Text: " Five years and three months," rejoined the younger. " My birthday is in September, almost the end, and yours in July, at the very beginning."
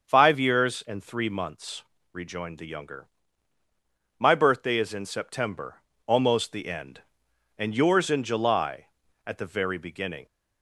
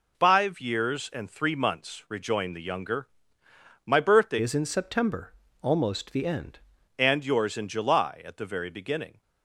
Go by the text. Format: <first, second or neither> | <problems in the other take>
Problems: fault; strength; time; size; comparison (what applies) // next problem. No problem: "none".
first | changes voice from "is" to "end"; from 4.4 to 6.5 s; 2.1 s long